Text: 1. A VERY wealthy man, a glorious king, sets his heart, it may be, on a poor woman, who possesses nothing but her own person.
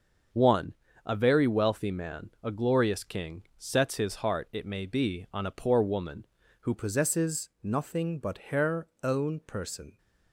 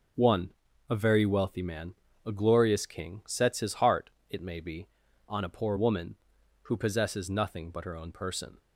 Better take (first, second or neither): second